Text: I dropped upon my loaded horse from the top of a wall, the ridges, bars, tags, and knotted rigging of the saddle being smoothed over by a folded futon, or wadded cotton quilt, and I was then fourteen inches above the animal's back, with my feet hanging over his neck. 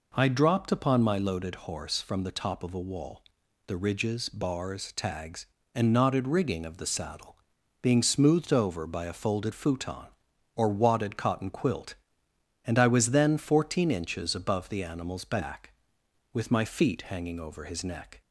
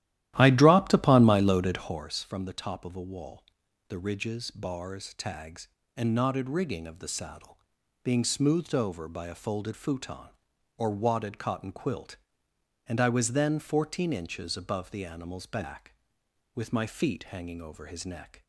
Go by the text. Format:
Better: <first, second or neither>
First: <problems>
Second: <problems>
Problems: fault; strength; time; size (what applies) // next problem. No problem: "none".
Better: first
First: pauses between "saddle" and "being"; noticeable; at 7.3 s; 0.50 s long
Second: starts louder than the rest; strong; until 2.0 s; 13.5 dB // pauses between "saddle" and "being"; noticeable; at 7.5 s; 0.50 s long